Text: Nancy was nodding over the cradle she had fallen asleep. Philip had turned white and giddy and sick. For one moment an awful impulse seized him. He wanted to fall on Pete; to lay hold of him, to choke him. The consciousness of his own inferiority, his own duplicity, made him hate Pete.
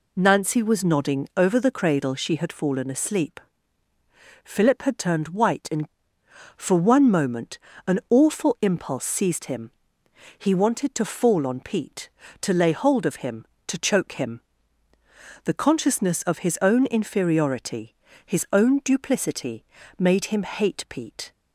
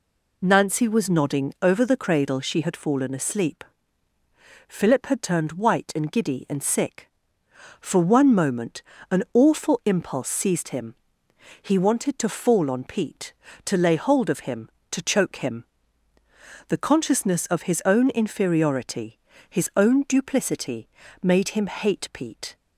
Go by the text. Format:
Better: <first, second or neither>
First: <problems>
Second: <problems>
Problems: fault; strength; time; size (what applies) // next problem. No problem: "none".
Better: second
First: skips "giddy and sick"; at 6.2 s // pauses between "moment" and "an"; slight; at 7.5 s; 0.26 s long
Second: pauses between "moment" and "an"; slight; at 8.8 s; 0.26 s long